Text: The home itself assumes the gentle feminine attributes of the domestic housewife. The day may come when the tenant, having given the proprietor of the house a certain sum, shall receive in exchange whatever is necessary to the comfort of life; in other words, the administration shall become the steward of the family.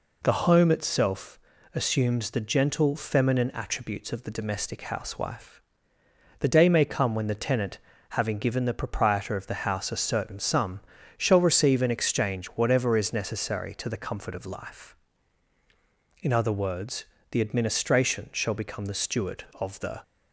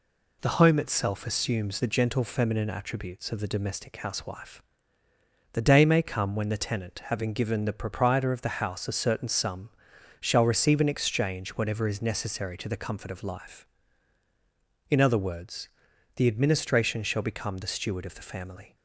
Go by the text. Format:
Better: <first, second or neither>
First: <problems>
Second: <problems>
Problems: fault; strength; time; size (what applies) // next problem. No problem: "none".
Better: second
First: pauses between "itself" and "assumes"; slight; at 1.3 s; 0.36 s long // stops before "family"; at 20.0 s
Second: none